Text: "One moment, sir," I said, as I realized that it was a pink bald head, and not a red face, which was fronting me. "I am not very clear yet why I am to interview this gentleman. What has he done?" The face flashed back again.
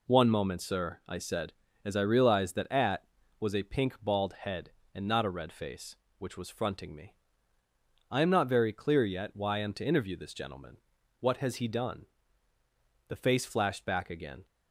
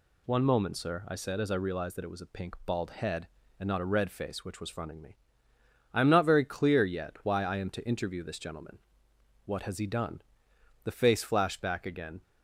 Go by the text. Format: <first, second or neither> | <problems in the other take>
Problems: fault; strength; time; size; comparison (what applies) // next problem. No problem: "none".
second | says "at" for "it"; at 2.7 s